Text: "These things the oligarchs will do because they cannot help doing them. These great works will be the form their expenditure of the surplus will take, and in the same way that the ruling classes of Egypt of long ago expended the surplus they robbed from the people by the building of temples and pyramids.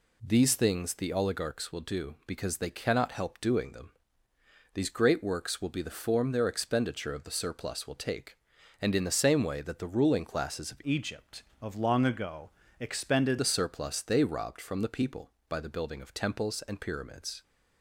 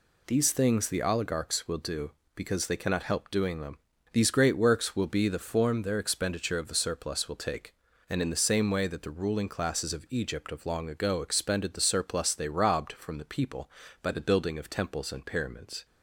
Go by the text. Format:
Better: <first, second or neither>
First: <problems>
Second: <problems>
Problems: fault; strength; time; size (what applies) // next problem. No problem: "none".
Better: second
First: changes voice from "Egypt" to "expended"; from 10.8 to 13.3 s; 2.5 s long // pauses between "ago" and "expended"; slight; at 12.5 s; 0.28 s long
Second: none